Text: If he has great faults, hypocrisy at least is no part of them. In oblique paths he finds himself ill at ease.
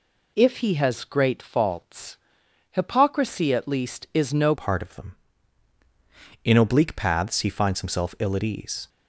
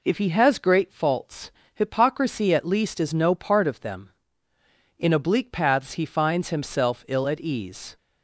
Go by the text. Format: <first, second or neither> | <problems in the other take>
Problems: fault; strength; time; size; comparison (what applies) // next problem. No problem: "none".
second | changes voice at "part"; from 4.5 s on; 4.3 s long